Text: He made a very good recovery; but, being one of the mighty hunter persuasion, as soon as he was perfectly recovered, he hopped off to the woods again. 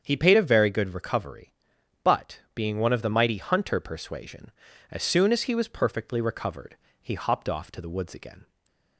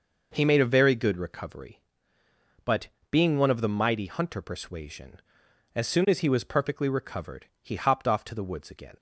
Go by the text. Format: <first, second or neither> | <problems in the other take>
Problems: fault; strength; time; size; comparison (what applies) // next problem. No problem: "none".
second | starts louder than the rest; strong; until 1.0 s; 7.5 dB // says "paid" for "made"; at 0.1 s // stays silent after the last word; slight; from 8.4 s on; 0.5 s long